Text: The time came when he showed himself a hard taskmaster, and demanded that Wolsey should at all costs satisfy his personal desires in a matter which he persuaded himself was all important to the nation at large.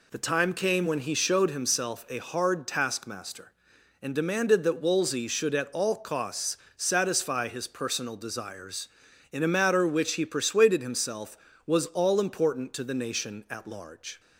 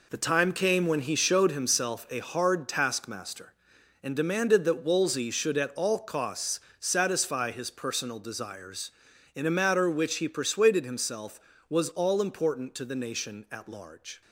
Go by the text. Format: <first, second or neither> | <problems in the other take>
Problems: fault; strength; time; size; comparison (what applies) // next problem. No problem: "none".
first | gets quieter; strong; throughout; 9 dB // pauses between "costs" and "satisfy"; slight; at 6.6 s; 0.18 s long; slight in the first